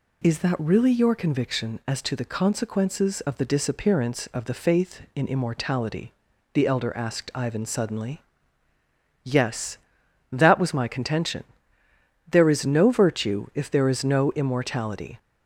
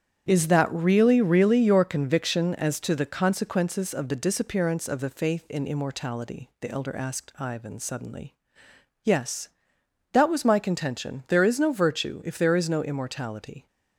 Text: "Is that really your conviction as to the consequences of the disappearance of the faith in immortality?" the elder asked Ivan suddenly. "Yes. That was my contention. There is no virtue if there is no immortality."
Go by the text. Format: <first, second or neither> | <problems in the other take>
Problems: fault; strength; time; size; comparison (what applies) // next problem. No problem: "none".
first | starts louder than the rest; strong; until 1.3 s; 9 dB // says "really" twice; at 1.2 s